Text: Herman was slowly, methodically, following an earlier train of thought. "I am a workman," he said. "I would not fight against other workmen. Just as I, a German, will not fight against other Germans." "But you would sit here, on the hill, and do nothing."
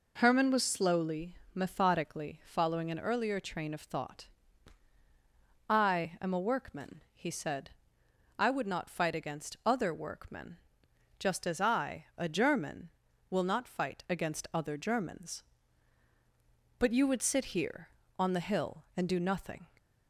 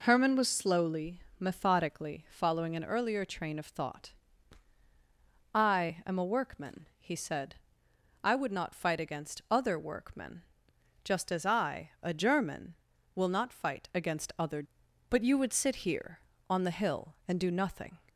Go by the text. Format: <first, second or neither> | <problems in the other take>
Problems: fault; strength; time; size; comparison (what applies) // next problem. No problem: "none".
first | skips "Germans"; at 14.8 s